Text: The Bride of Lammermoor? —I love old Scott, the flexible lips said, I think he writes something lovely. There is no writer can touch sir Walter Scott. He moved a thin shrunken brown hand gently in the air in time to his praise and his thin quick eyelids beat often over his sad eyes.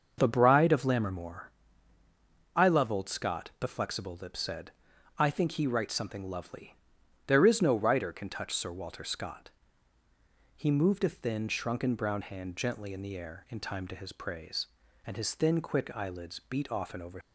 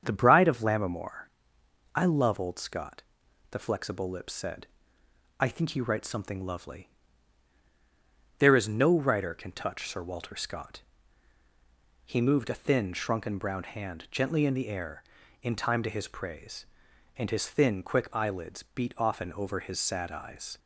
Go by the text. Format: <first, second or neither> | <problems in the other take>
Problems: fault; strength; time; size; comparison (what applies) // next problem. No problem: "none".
second | starts louder than the rest; until 1.1 s; 6.5 dB; strong in the second // stops before "his sad eyes"; at 17.2 s